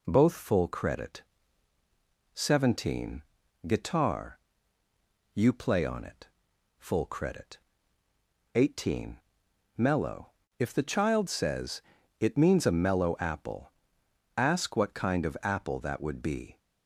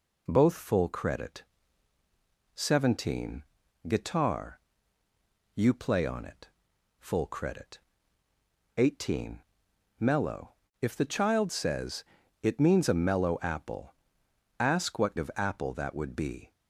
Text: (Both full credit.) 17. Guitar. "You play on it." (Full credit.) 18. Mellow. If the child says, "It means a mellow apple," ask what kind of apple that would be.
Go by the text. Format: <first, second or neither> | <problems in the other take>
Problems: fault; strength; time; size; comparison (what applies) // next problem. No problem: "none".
first | skips "kind"; at 15.1 s